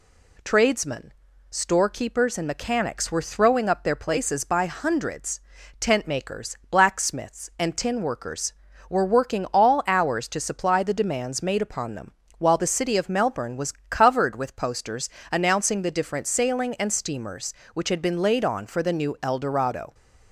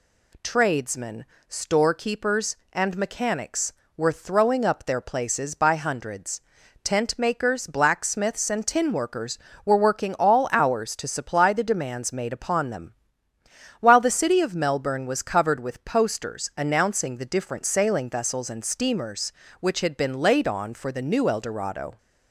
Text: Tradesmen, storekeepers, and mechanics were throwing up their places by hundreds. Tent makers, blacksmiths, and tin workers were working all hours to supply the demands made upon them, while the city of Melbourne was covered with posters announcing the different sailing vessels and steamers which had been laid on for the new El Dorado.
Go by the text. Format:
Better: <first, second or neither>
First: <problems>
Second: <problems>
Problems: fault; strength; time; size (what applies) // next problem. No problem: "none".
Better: second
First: pauses between "was" and "covered"; slight; at 13.7 s; 0.18 s long // pauses between "posters" and "announcing"; slight; at 15.0 s; 0.24 s long // skips "vessels"; at 16.7 s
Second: none